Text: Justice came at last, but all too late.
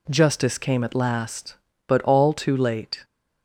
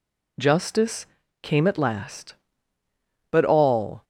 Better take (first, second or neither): first